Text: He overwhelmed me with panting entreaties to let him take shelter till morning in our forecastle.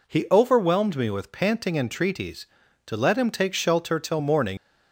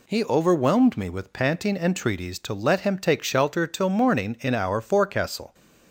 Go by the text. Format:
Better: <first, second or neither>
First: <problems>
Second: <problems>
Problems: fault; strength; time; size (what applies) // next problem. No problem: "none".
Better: second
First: stops before "in our forecastle"; at 4.5 s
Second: none